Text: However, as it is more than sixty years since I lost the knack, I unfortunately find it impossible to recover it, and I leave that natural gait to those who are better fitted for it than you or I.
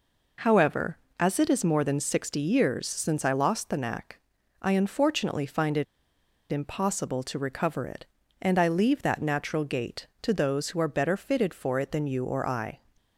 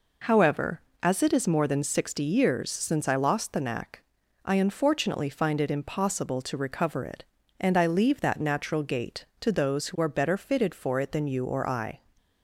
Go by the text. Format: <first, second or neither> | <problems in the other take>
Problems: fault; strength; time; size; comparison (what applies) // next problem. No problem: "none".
second | pauses between "it" and "impossible"; noticeable; at 5.8 s; 0.65 s long